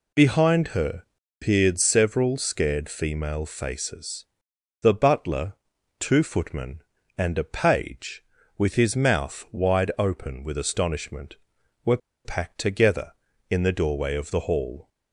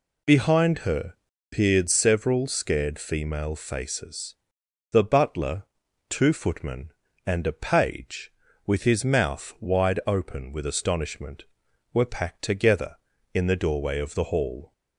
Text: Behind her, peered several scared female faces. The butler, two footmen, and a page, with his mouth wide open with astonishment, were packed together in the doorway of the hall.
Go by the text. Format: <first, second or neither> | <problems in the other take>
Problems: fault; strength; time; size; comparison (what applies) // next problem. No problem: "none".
second | pauses between "were" and "packed"; slight; at 11.9 s; 0.27 s long